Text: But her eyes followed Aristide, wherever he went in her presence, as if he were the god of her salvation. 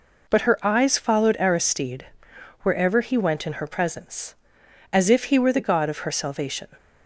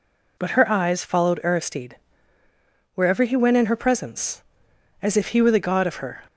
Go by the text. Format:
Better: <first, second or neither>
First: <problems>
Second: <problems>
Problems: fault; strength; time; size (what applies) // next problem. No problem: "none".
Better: first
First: none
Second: stops before "salvation"; at 6.2 s